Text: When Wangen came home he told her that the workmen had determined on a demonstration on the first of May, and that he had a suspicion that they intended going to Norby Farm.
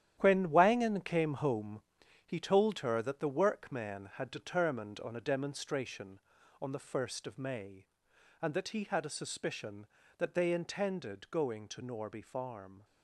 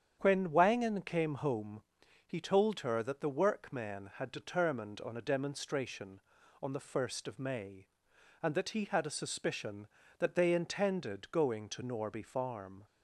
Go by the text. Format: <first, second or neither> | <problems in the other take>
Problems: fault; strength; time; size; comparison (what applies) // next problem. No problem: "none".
second | gets quieter; strong; throughout; 9.5 dB // starts louder than the rest; strong; until 1.2 s; 10.5 dB; strong in the second // pauses between "home" and "he"; at 1.8 s; 0.44 s long; also in the second